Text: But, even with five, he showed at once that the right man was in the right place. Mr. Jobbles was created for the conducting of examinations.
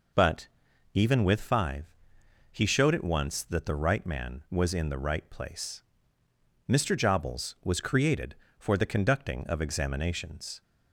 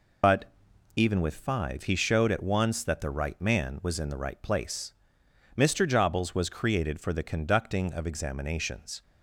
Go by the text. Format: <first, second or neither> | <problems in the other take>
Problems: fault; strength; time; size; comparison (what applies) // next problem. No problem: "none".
first | loses the start of "But"; at 0.2 s; 80 ms